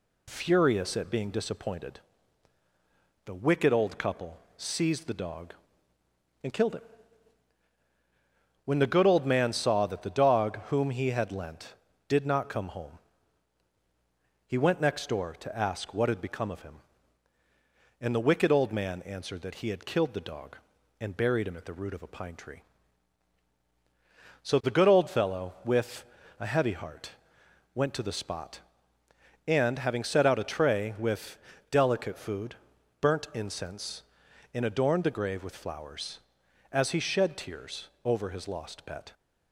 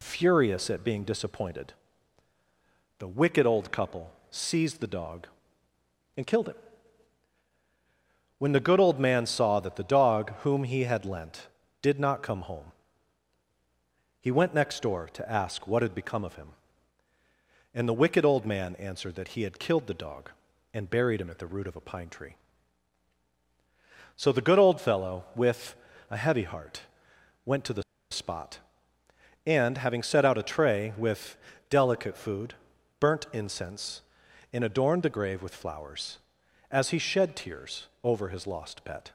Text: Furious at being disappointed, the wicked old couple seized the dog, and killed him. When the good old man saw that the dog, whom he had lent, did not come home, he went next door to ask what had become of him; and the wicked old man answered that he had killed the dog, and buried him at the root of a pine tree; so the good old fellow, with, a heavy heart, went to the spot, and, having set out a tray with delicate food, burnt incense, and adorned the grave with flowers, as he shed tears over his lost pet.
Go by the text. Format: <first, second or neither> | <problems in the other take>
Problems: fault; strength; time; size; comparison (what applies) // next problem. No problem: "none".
first | pauses between "couple" and "seized"; slight; at 4.1 s; 0.22 s long; slight in the first // pauses between "the" and "spot"; slight; at 27.8 s; 0.29 s long // pauses between "with" and "delicate"; slight; at 31.3 s; 0.36 s long; slight in the first // pauses between "tears" and "over"; slight; at 37.8 s; 0.18 s long; slight in the first